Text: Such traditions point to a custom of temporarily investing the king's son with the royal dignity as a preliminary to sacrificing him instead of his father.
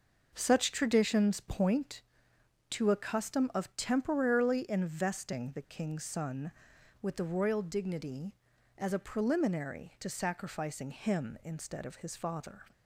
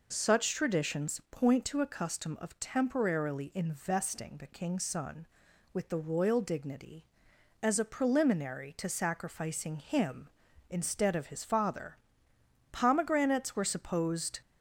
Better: first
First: none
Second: goes on to say "Pomegranates were supposed"; strong; from 12.7 s on; 1.6 s long

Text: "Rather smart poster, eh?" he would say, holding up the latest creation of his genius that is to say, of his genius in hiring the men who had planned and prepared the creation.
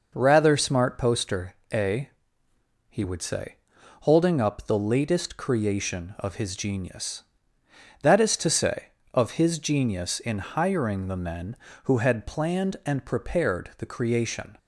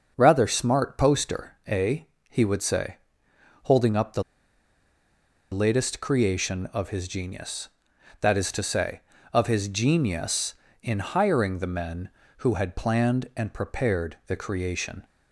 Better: first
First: none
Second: starts louder than the rest; until 1.1 s; 6.5 dB // pauses between "the" and "latest"; strong; at 4.2 s; 1.2 s long

